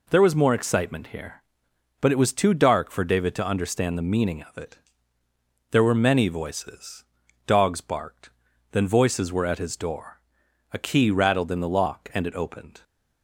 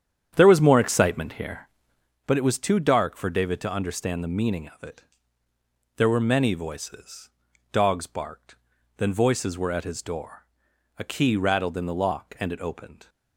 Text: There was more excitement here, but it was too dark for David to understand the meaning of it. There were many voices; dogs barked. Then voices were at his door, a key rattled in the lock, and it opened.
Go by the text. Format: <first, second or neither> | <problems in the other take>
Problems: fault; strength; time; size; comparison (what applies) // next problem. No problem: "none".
first | starts louder than the rest; strong; until 2.2 s; 9 dB